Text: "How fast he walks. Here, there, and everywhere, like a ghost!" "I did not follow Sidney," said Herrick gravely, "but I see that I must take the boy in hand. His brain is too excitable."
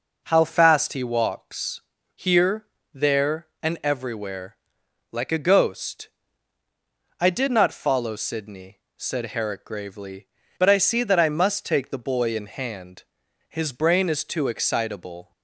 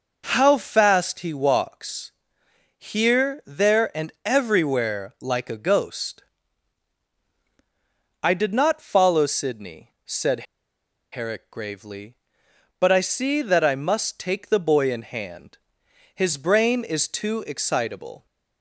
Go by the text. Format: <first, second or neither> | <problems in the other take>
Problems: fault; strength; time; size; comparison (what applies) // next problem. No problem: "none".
first | pauses between "said" and "Herrick"; noticeable; at 10.4 s; 0.74 s long